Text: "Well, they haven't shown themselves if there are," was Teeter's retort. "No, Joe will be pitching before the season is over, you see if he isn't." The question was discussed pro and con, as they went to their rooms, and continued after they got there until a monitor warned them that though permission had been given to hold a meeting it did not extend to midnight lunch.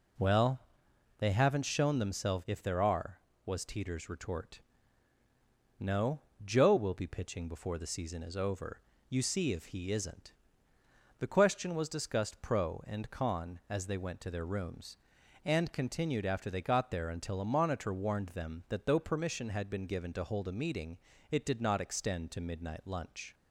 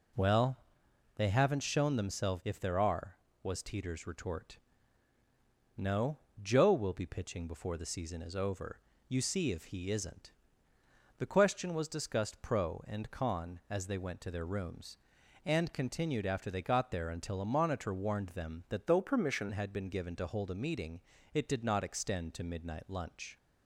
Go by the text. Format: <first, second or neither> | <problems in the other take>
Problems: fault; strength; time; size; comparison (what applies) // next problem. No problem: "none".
first | changes voice from "though" to "permission"; from 18.8 to 19.5 s; 0.7 s long // pauses between "meeting" and "it"; slight; at 21.0 s; 0.34 s long; slight in the first